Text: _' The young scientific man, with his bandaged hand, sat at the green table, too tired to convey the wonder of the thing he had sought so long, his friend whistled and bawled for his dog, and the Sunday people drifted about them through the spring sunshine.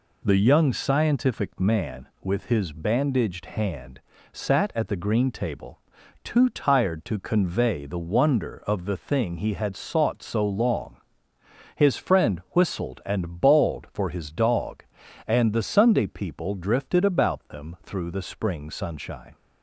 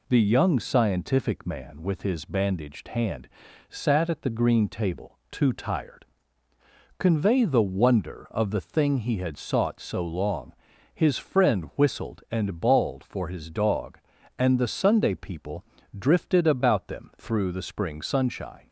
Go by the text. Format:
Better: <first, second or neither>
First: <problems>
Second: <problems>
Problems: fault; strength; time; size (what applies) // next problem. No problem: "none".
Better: first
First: none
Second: skips "to"; at 6.5 s // pauses between "people" and "drifted"; slight; at 15.6 s; 0.36 s long